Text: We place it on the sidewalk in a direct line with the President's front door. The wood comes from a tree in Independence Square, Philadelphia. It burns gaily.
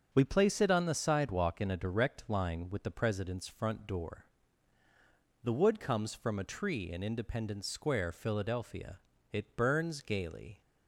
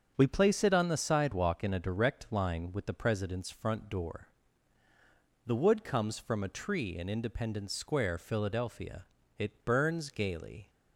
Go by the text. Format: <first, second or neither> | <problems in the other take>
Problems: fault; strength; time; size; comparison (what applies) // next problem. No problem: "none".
neither | starts louder than the rest; the same in both